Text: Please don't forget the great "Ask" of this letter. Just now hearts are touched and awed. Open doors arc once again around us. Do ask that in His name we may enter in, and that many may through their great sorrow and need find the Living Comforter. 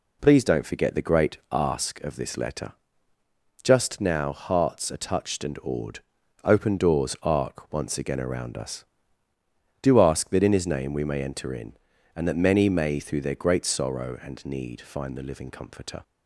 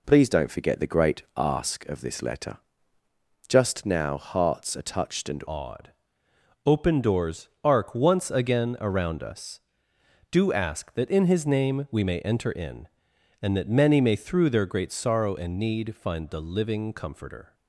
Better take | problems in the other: first | changes voice at "awed"; from 5.4 s on; 12.1 s long // pauses between "doors" and "arc"; slight; at 7.4 s; 0.16 s long

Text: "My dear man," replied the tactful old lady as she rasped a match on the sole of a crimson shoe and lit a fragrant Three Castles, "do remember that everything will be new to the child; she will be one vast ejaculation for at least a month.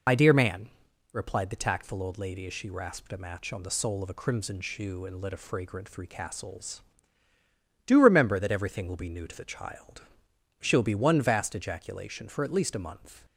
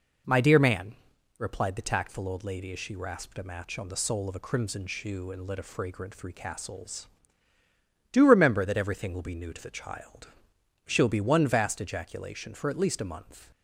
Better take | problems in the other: second | loses the start of "My"; at 0.0 s; 60 ms

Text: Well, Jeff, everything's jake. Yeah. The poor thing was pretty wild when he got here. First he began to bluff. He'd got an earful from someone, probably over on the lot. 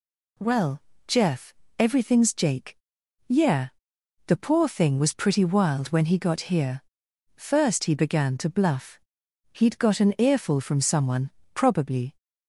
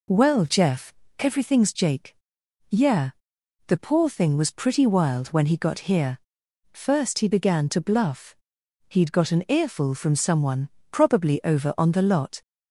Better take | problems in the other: second | stops before "over on the lot"; at 12.1 s

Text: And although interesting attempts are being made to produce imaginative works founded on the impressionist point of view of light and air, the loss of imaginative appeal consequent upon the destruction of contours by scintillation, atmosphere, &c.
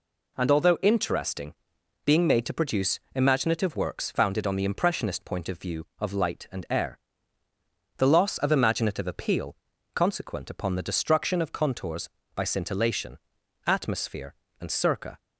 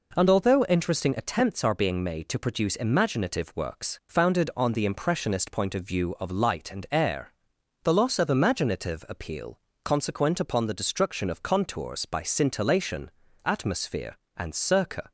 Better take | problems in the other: second | skips "attempts are"; at 1.7 s // pauses between "produce" and "imaginative"; slight; at 2.9 s; 0.16 s long // pauses between "appeal" and "consequent"; at 9.5 s; 0.38 s long; slight in the second

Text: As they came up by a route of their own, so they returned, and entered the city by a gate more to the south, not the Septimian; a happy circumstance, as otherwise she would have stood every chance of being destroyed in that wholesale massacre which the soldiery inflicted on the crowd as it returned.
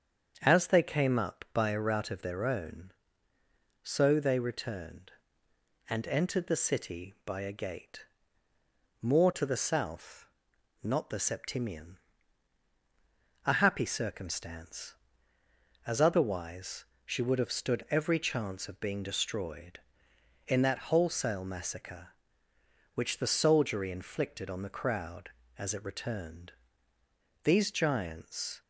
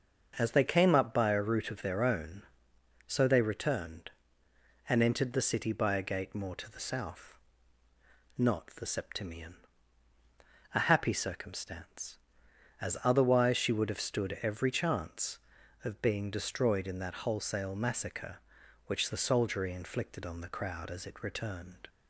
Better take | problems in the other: second | starts louder than the rest; strong; until 1.4 s; 7.5 dB; also in the second // pauses between "gate" and "more"; noticeable; at 8.0 s; 0.96 s long // pauses between "otherwise" and "she"; slight; at 16.8 s; 0.18 s long // goes on to say "These giants"; noticeable; from 27.4 s on; 1.1 s long

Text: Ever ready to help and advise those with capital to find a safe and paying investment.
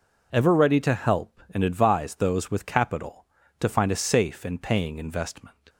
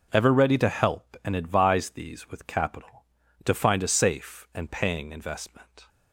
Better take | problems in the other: first | says "these" for "those"; at 1.9 s

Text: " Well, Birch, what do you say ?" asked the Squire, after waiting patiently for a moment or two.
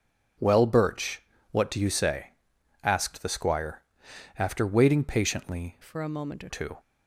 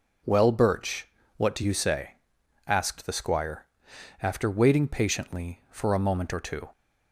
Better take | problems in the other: second | changes voice from "for" to "or"; from 5.8 to 6.4 s; 0.6 s long

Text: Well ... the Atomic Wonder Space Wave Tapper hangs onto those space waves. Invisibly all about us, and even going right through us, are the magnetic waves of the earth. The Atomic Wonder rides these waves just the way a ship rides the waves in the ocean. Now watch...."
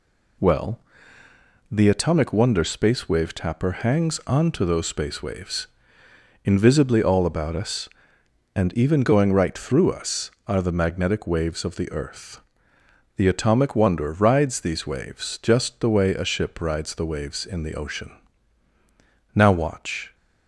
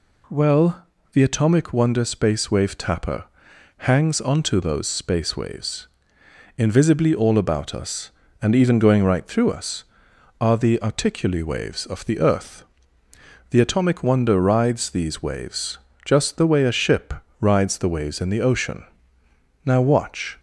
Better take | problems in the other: first | pauses between "Tapper" and "hangs"; noticeable; at 3.2 s; 0.52 s long // says "articuli" for "magnetic"; at 10.7 s // pauses between "waves" and "just"; slight; at 15.7 s; 0.26 s long // pauses between "ship" and "rides"; slight; at 17.1 s; 0.26 s long

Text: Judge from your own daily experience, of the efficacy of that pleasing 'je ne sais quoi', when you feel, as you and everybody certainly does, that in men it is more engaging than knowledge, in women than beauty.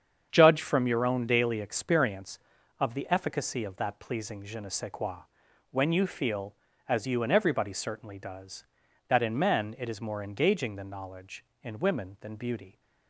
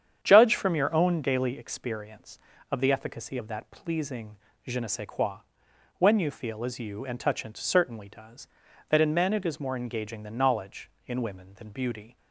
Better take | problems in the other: first | starts louder than the rest; strong; until 1.2 s; 8.5 dB; strong in the first // pauses between "pleasing" and "je"; slight; at 4.3 s; 0.30 s long // says "touchant" for "everybody"; at 7.2 s

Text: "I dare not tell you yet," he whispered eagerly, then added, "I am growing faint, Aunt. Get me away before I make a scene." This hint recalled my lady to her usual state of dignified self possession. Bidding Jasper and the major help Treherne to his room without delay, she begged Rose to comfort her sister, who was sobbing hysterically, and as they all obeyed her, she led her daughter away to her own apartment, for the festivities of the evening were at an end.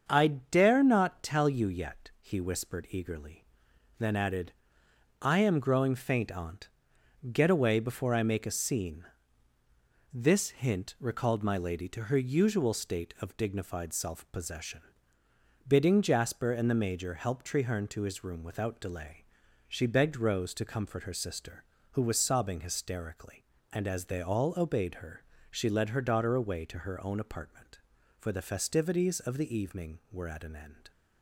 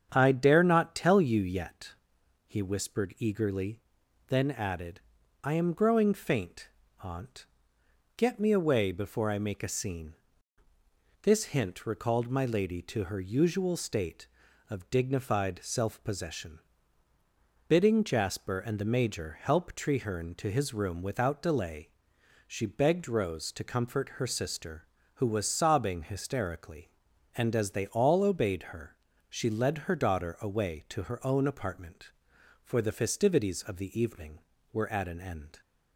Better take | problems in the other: second | starts louder than the rest; until 1.0 s; 7 dB; strong in the second // skips "me"; at 7.5 s

